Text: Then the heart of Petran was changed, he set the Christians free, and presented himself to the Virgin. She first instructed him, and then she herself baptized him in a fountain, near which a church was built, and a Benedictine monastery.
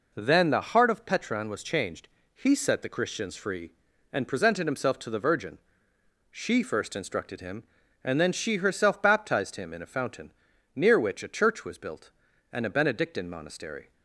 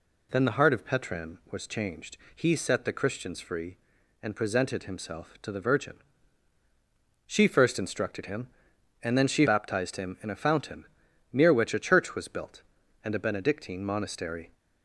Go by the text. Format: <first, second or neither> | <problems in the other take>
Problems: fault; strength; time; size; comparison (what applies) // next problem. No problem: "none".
first | skips "herself"; at 9.4 s